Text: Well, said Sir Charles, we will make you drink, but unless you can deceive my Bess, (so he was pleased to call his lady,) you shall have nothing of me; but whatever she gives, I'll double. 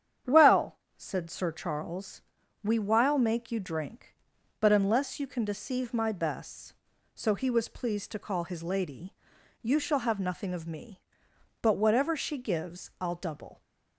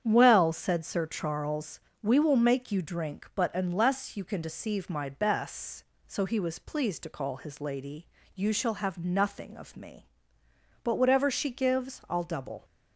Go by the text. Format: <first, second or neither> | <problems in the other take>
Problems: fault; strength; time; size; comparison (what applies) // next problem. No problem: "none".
second | starts louder than the rest; strong; until 1.4 s; 9 dB; strong in the second // says "while" for "will"; at 2.7 s